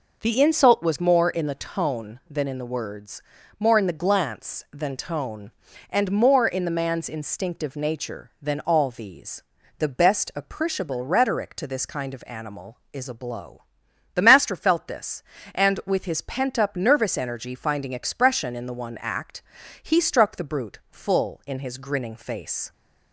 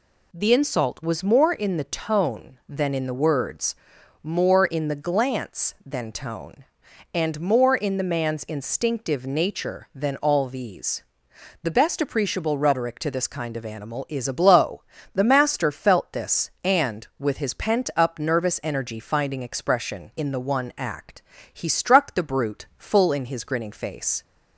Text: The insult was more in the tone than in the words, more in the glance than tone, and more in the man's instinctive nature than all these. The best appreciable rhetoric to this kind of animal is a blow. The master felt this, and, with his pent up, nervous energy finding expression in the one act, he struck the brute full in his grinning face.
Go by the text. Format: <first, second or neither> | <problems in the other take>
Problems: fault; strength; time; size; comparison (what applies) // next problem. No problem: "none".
neither | none